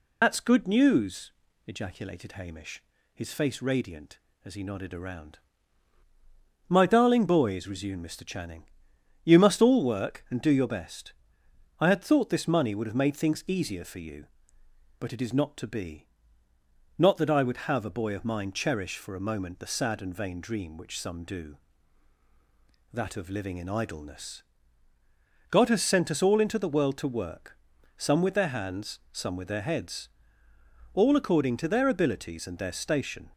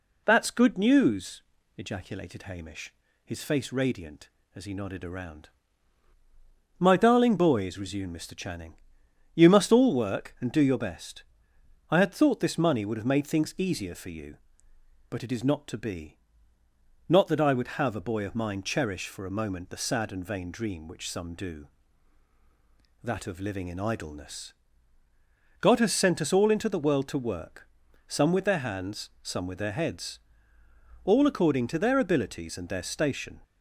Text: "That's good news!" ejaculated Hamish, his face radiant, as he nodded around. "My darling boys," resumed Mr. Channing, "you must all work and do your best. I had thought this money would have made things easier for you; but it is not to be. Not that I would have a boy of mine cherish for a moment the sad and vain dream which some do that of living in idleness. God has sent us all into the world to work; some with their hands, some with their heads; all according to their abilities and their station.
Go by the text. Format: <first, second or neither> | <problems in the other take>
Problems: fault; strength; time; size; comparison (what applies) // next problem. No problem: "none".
second | loses the start of "That's"; at 0.2 s; 65 ms